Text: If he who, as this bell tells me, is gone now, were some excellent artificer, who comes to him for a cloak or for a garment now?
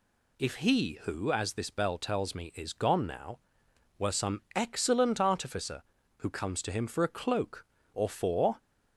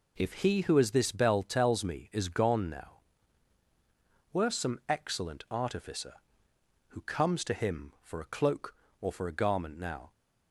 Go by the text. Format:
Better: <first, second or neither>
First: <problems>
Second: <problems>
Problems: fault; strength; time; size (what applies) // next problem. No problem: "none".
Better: second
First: stops before "a garment now"; at 8.5 s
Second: none